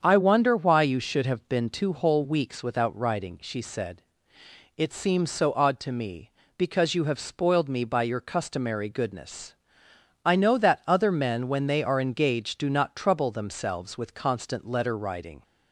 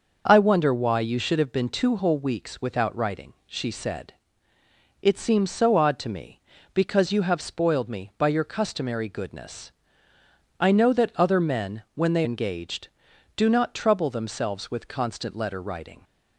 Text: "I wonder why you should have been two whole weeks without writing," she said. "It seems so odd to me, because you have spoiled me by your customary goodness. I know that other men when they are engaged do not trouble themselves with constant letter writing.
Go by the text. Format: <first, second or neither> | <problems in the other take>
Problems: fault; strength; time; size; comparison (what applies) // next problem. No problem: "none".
first | starts louder than the rest; noticeable; until 1.3 s; 6 dB; strong in the first // skips "are"; at 12.2 s